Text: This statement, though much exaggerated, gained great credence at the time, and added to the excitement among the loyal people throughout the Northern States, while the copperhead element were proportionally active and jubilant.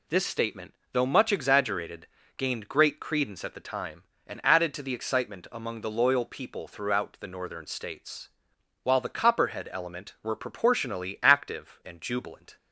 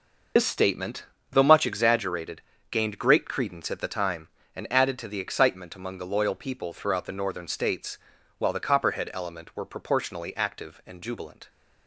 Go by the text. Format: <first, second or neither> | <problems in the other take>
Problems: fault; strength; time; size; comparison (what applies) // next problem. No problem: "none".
first | loses the start of "This"; at 0.3 s; 90 ms